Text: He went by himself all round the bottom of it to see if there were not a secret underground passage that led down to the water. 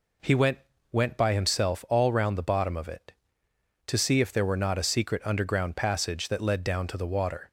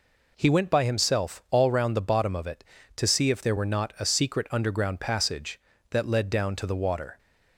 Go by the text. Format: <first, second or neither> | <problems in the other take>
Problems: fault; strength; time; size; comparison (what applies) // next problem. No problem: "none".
second | says "went" twice; at 0.9 s